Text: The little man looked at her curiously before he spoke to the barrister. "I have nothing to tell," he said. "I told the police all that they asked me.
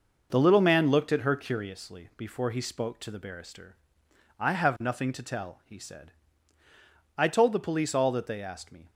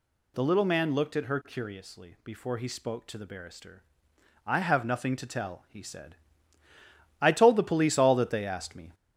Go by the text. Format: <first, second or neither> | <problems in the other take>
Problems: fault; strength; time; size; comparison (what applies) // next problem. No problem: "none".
first | gets louder; throughout; 3.5 dB